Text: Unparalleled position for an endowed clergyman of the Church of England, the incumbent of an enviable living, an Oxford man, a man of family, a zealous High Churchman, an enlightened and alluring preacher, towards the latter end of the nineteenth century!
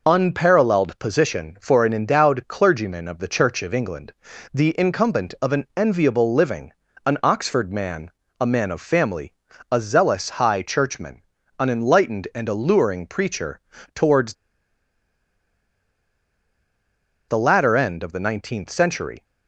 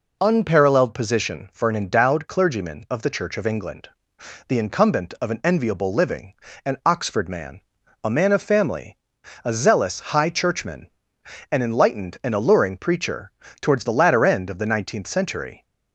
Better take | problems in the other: second | pauses between "towards" and "the"; strong; at 14.3 s; 2.9 s long

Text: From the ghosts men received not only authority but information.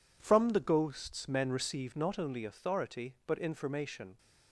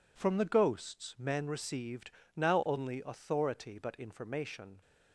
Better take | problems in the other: first | says "now" for "not"; at 2.3 s

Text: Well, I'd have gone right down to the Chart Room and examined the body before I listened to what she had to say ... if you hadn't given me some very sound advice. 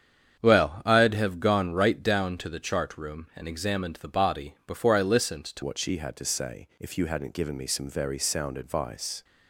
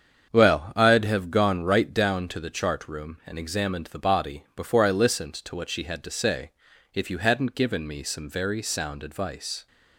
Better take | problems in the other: second | starts louder than the rest; strong; until 1.4 s; 8 dB; strong in the second // changes voice at "what"; from 5.6 s on; 3.6 s long

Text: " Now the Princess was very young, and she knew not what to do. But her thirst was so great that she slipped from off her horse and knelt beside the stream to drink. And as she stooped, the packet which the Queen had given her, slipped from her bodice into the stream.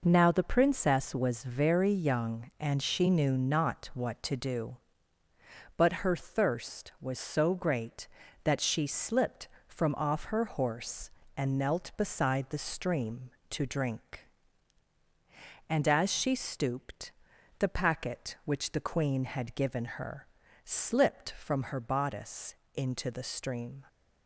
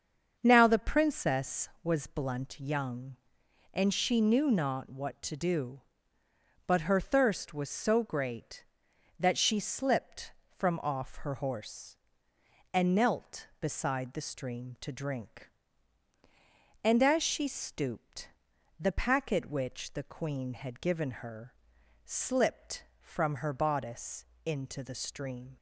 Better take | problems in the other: first | starts louder than the rest; until 1.3 s; 7 dB // says "blunt" for "very"; at 2.0 s // pauses between "bodice" and "into"; slight; at 24.2 s; 0.18 s long; slight in the first

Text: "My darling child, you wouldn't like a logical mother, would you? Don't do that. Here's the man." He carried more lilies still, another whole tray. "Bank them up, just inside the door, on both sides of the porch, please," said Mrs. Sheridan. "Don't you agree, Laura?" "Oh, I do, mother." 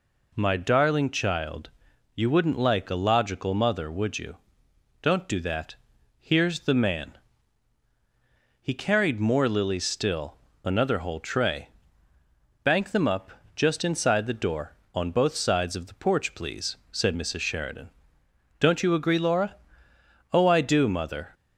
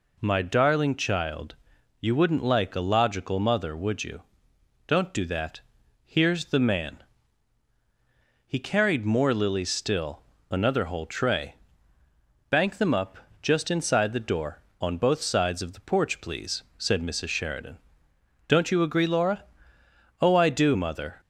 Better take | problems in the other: neither | none

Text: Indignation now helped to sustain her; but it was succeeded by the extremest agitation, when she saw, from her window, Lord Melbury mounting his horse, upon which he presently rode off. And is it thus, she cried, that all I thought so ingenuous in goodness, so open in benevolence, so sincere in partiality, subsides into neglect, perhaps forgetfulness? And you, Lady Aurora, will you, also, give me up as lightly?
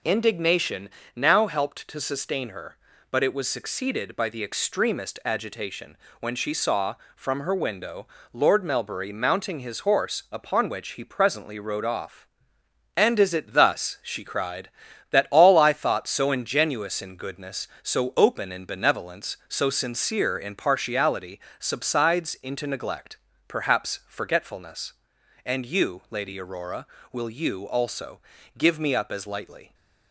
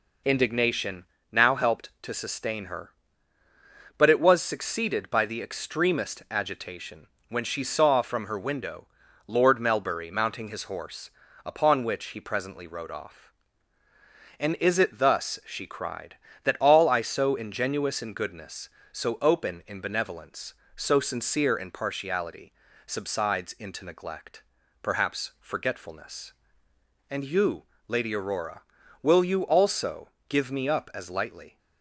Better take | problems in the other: first | pauses between "Indignation" and "now"; slight; at 1.0 s; 0.26 s long; slight in the first // skips "thought"; at 17.0 s

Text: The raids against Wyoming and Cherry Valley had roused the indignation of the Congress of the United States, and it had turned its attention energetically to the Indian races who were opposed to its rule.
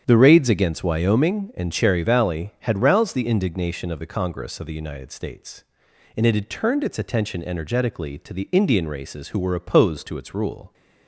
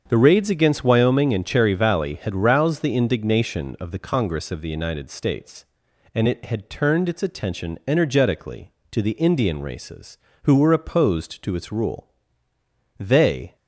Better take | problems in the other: first | starts louder than the rest; strong; until 1.0 s; 7.5 dB; strong in the first // goes on to say "They"; from 12.9 s on; 0.56 s long

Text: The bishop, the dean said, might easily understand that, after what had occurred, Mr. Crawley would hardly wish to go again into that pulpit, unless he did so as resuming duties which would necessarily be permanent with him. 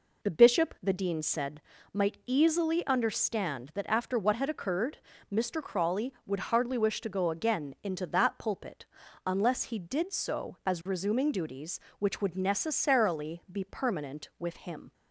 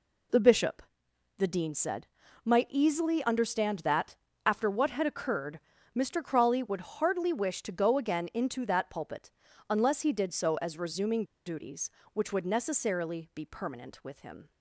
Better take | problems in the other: first | pauses between "resuming" and "duties"; slight; at 11.2 s; 0.21 s long

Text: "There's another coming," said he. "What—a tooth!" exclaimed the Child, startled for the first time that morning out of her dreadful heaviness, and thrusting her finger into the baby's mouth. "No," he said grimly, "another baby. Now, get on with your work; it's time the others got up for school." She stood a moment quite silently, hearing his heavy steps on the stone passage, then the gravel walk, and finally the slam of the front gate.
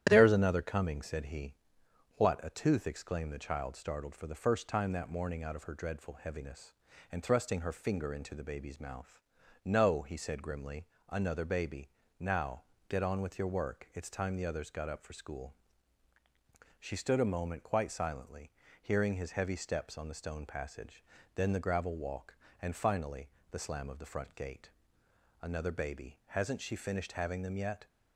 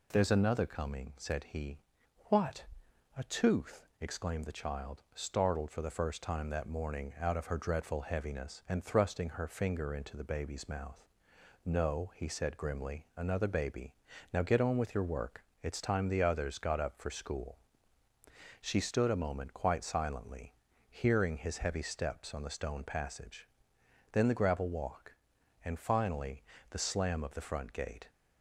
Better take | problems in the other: second | starts louder than the rest; strong; until 1.1 s; 11 dB // pauses between "finally" and "the"; slight; at 23.2 s; 0.22 s long; slight in the second // goes on to say "Another baby Hasn't she finished having them yet"; strong; from 25.4 s on; 2.4 s long

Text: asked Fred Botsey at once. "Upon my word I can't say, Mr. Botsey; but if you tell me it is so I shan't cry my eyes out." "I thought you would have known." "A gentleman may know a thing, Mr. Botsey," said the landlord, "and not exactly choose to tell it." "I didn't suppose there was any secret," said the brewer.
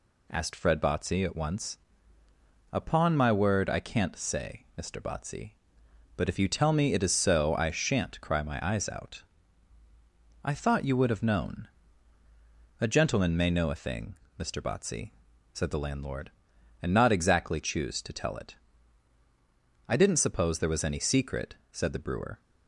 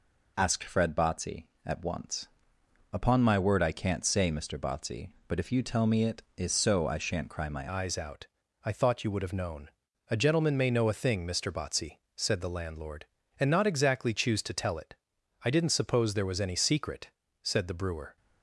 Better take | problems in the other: first | changes voice at "eyes"; from 7.6 s on; 10.5 s long

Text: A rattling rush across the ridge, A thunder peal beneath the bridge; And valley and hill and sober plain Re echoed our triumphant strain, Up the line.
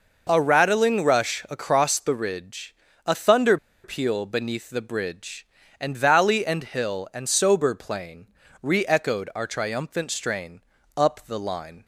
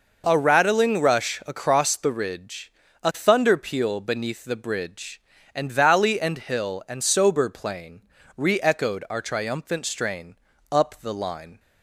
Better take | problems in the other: second | pauses between "thunder" and "peal"; slight; at 3.5 s; 0.27 s long // pauses between "plain" and "Re"; slight; at 8.2 s; 0.34 s long; slight in the second

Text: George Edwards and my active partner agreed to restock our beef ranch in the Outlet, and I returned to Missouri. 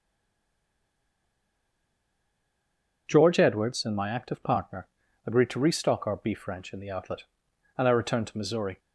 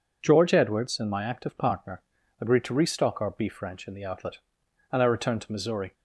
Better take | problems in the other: second | stays silent before the first word; strong; until 3.0 s; 3.0 s long // pauses between "partner" and "agreed"; at 4.8 s; 0.40 s long; also in the second

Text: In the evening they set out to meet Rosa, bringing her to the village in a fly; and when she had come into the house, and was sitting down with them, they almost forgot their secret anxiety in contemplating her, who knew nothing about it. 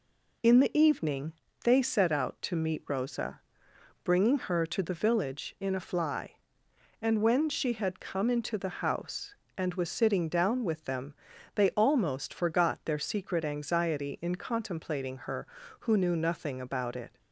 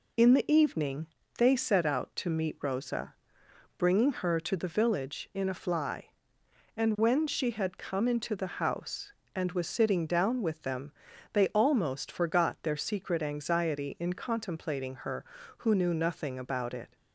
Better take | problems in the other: neither | pauses between "evening" and "they"; slight; the same in both

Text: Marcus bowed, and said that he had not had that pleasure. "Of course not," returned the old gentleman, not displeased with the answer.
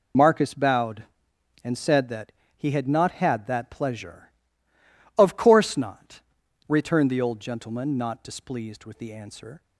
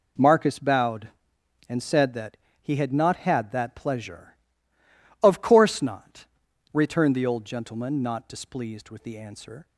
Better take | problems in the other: second | loses the start of "Marcus"; at 0.1 s; 35 ms // pauses between "that" and "he"; slight; at 2.3 s; 0.24 s long; slight in the second

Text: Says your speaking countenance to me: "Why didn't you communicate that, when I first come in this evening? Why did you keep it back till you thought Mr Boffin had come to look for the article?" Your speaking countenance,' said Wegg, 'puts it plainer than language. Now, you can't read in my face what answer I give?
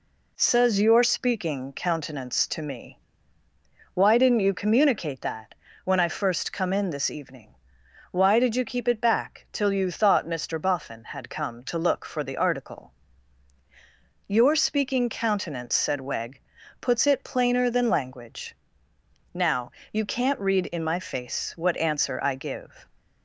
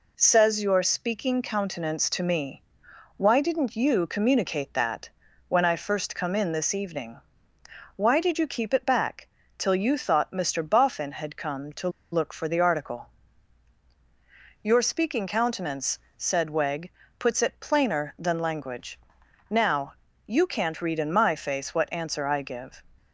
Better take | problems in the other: first | pauses between "back" and "till"; slight; at 9.2 s; 0.30 s long // pauses between "to" and "look"; slight; at 11.8 s; 0.23 s long

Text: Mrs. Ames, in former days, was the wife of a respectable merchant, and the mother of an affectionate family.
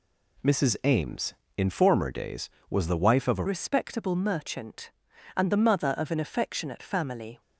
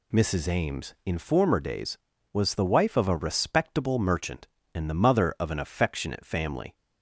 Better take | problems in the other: second | changes voice at "respectable"; from 3.4 s on; 4.0 s long

